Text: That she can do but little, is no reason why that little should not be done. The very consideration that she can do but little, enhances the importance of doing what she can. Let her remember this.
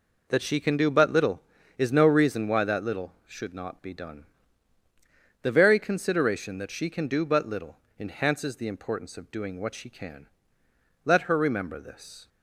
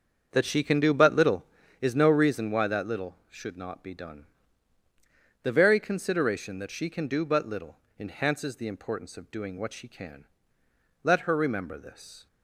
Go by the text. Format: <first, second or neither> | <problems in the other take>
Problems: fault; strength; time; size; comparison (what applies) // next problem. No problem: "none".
first | starts louder than the rest; until 1.9 s; 7 dB